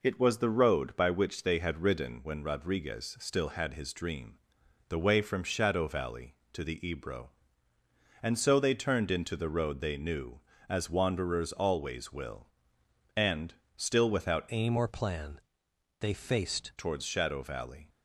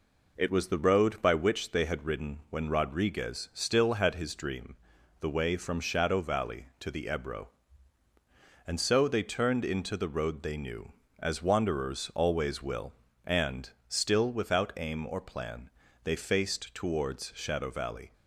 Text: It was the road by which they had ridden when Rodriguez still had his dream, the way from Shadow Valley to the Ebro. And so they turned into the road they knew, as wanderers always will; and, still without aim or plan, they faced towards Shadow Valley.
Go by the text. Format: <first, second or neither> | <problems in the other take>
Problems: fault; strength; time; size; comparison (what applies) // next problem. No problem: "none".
second | changes voice from "aim" to "faced"; from 14.5 to 16.7 s; 2.2 s long